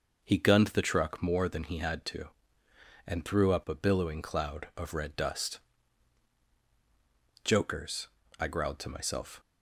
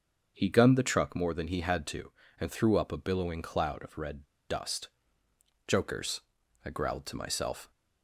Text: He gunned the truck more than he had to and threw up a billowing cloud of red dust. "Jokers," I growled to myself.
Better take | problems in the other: first | starts louder than the rest; until 1.3 s; 6.5 dB // pauses between "red" and "dust"; slight; at 4.2 s; 0.23 s long

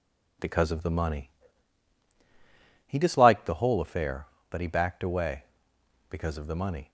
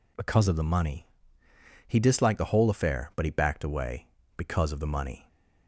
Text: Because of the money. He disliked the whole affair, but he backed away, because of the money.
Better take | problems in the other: neither | none

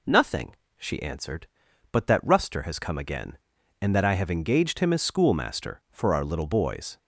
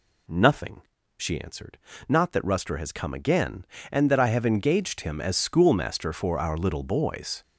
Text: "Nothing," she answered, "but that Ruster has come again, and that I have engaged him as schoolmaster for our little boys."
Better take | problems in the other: first | says "not" for "but"; at 2.0 s

